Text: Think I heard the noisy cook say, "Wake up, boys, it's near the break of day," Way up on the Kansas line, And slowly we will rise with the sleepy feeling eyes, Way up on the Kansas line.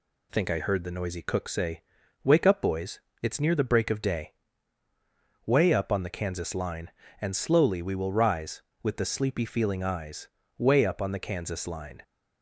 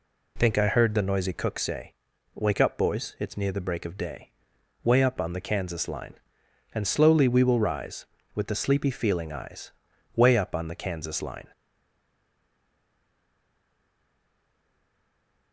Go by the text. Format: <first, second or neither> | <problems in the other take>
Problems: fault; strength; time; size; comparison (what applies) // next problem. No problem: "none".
first | stays silent after the last word; strong; from 11.5 s on; 4.0 s long